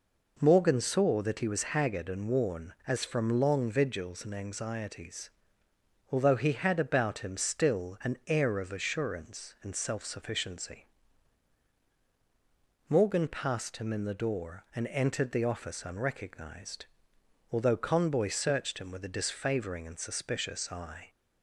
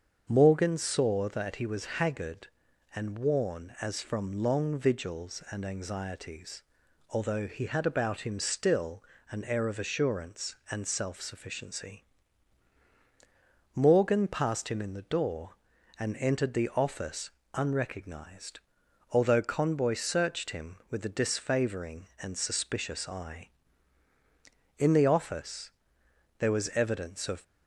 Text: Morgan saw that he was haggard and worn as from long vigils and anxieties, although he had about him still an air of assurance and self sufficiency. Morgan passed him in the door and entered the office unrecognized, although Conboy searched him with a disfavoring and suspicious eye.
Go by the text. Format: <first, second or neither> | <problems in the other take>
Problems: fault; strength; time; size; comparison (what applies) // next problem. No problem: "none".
first | starts louder than the rest; until 1.2 s; 7 dB // pauses between "still" and "an"; slight; at 9.0 s; 0.28 s long // pauses between "office" and "unrecognized"; slight; at 17.3 s; 0.24 s long // goes on to say "In the office there was evidence of"; strong; from 24.7 s on; 2.6 s long